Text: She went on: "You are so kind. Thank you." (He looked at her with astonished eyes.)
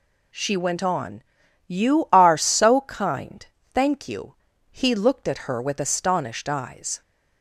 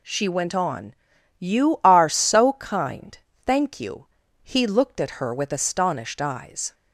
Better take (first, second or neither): neither